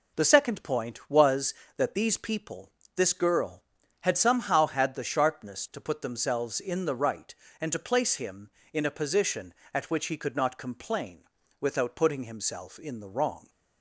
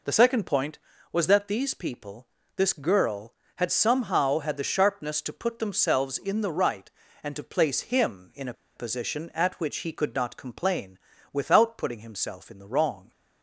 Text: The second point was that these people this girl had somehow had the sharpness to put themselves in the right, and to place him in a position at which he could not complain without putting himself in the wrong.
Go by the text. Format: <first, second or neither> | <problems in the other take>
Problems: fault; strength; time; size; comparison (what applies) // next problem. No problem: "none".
first | pauses between "people" and "this"; slight; at 2.2 s; 0.30 s long; slight in the first // pauses between "a" and "position"; slight; at 8.5 s; 0.22 s long // pauses between "complain" and "without"; slight; at 10.9 s; 0.36 s long; slight in the first